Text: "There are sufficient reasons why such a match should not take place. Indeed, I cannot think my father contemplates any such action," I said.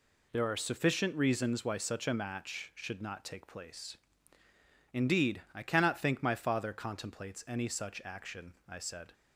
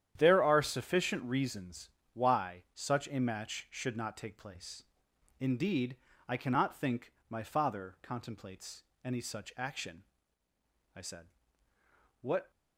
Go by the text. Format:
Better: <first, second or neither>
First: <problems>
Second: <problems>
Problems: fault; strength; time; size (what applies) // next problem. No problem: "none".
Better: first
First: none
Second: starts louder than the rest; strong; until 1.1 s; 10 dB // pauses between "reasons" and "why"; slight; at 1.9 s; 0.24 s long // pauses between "think" and "my"; slight; at 7.1 s; 0.16 s long // pauses between "contemplates" and "any"; slight; at 8.8 s; 0.22 s long // goes on to say "What"; slight; from 12.2 s on; 0.28 s long